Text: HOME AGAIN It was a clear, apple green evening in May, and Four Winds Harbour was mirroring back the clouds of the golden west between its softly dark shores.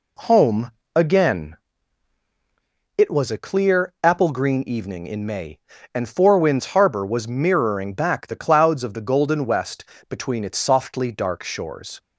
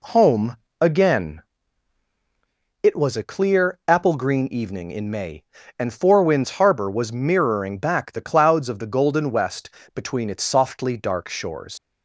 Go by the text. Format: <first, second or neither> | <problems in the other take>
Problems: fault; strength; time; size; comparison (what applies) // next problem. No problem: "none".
first | pauses between "HOME" and "AGAIN"; slight; at 0.5 s; 0.24 s long; slight in the first // pauses between "AGAIN" and "It"; strong; at 1.4 s; 1.4 s long; strong in the first // pauses between "west" and "between"; slight; at 9.7 s; 0.24 s long; slight in the first // leaves "shores" unfinished; at 11.7 s; 85 ms